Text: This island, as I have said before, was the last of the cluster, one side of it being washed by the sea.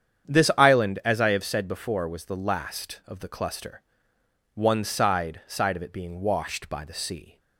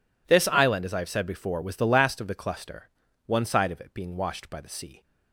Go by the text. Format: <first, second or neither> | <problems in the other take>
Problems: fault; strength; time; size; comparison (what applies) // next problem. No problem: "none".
second | starts louder than the rest; strong; until 1.3 s; 8.5 dB // says "side" twice; at 5.4 s